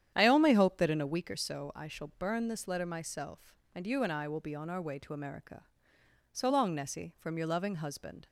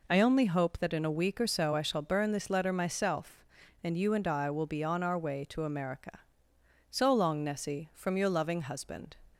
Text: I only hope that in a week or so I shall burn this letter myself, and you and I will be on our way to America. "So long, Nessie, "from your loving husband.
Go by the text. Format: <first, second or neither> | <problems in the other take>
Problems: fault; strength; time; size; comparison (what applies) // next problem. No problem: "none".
second | starts louder than the rest; strong; until 1.1 s; 9.5 dB